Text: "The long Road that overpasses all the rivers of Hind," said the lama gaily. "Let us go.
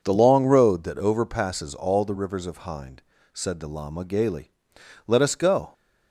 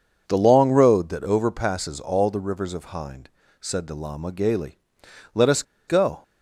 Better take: first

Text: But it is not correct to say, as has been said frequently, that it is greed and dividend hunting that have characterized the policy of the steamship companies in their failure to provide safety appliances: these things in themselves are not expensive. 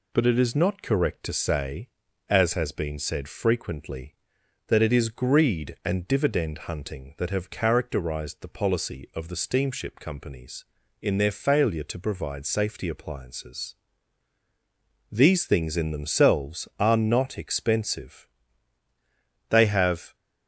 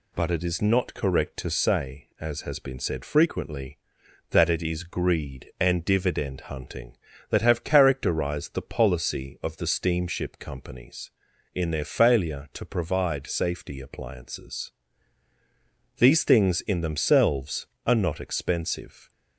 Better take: second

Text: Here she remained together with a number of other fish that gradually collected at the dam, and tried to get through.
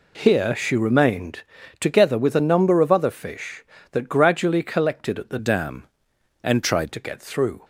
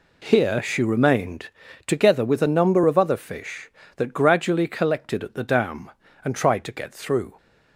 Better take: second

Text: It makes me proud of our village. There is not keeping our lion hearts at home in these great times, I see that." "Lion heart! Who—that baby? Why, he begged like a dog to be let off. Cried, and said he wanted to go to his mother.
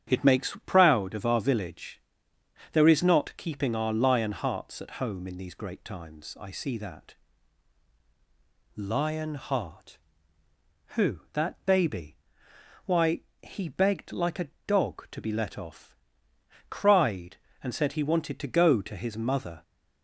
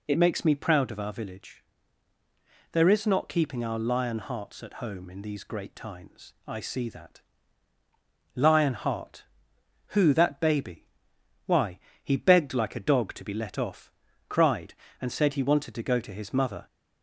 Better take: second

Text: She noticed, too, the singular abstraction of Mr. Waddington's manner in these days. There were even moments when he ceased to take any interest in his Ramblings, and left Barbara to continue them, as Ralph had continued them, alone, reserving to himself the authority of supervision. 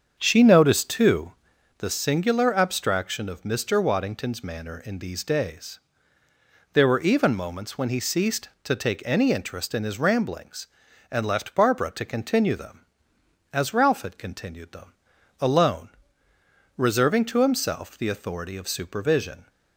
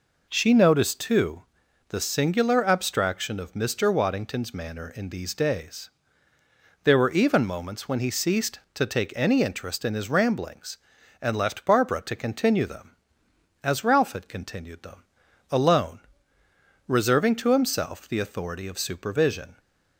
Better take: second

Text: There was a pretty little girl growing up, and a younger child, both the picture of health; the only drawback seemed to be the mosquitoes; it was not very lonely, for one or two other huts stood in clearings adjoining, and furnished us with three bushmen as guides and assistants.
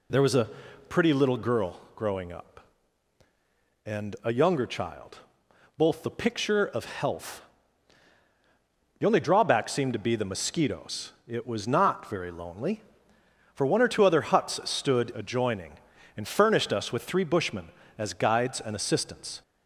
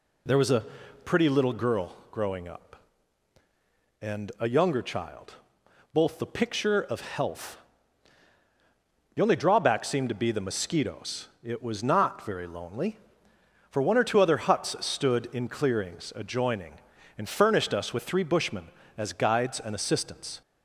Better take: second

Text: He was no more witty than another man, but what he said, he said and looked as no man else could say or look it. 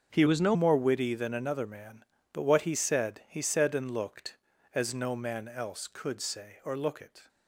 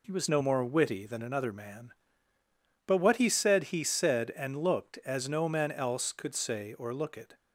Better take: second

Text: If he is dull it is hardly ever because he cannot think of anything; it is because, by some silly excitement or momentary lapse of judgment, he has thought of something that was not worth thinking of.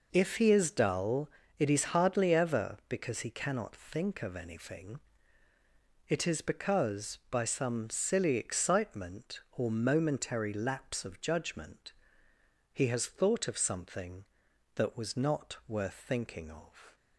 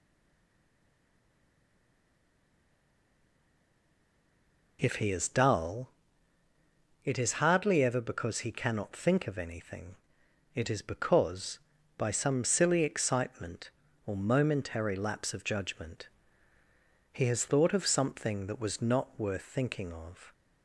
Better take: first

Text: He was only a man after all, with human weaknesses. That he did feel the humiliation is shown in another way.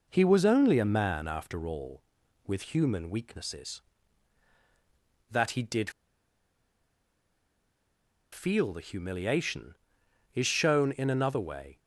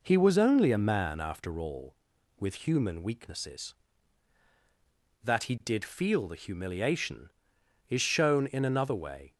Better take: second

